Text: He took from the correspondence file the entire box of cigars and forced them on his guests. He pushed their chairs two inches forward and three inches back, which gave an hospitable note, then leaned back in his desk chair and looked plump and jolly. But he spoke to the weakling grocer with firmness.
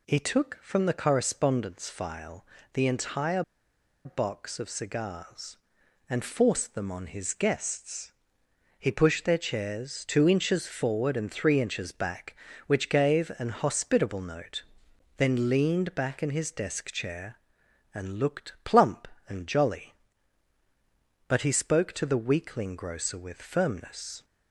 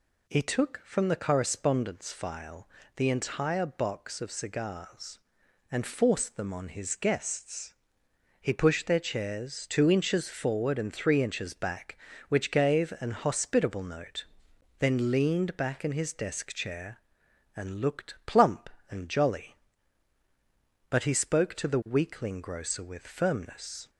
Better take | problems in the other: second | pauses between "file" and "the"; slight; at 2.4 s; 0.28 s long; slight in the second // pauses between "entire" and "box"; noticeable; at 3.4 s; 0.63 s long

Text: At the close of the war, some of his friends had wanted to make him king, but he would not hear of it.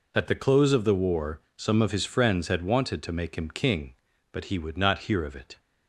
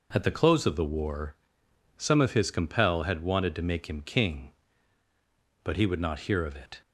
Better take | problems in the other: first | says "compel" for "friends"; at 2.5 s

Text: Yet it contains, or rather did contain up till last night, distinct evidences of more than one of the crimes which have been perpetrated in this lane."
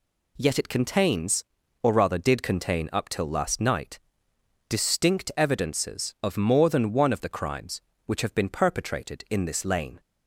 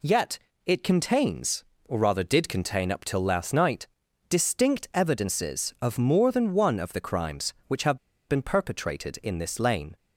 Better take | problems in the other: first | pauses between "Yet" and "it"; slight; at 0.3 s; 0.28 s long // pauses between "have" and "been"; slight; at 7.9 s; 0.30 s long

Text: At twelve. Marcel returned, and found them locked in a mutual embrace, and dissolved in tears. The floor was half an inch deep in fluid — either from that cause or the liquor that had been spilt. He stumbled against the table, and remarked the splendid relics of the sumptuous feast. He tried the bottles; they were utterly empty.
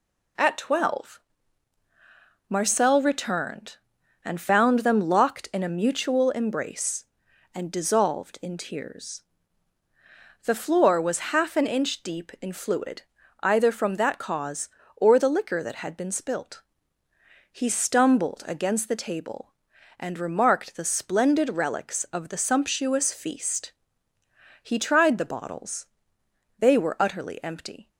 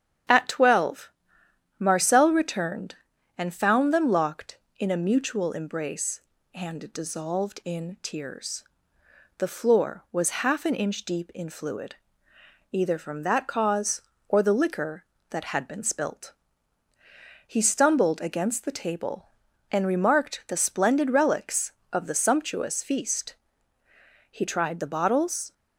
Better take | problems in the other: first | starts louder than the rest; strong; until 1.9 s; 9 dB // stops before "they were utterly empty"; at 25.5 s

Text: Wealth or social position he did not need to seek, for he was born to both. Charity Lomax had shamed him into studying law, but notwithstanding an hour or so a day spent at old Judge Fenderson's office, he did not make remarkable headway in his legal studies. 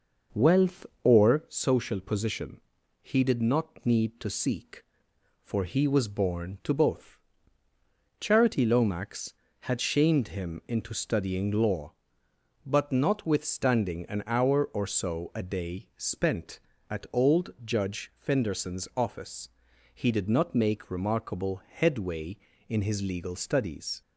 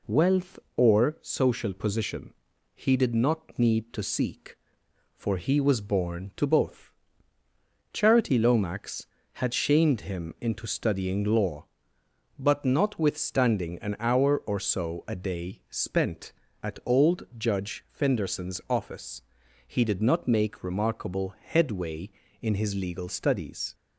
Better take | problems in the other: second | starts louder than the rest; noticeable; until 1.7 s; 5.5 dB // pauses between "position" and "he"; at 2.6 s; 0.40 s long; also in the second

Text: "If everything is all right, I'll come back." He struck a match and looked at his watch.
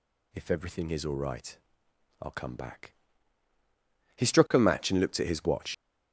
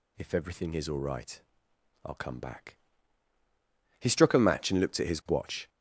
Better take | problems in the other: second | leaves "watch" unfinished; at 5.7 s; 100 ms

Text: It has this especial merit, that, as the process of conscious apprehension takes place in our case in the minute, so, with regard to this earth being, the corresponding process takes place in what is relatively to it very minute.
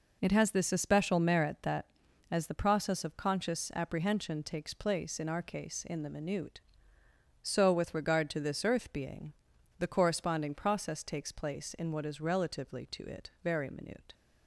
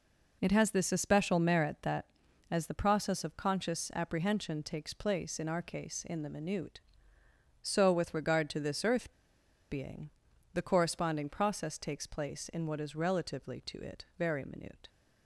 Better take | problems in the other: first | pauses between "earth" and "being"; noticeable; at 9.1 s; 0.59 s long

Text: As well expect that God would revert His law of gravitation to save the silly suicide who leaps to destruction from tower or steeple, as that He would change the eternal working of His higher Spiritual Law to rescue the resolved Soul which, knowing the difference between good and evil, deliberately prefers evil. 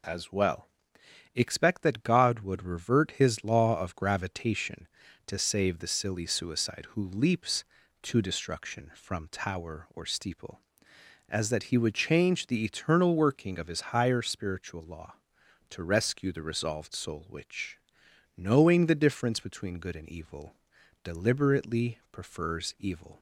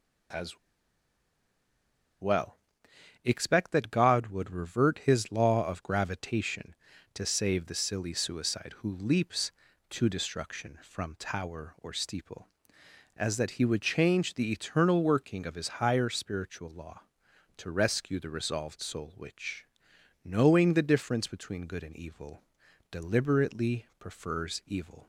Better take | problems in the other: first | pauses between "As" and "well"; strong; at 0.5 s; 1.6 s long // pauses between "well" and "expect"; noticeable; at 2.5 s; 0.68 s long; noticeable in the first

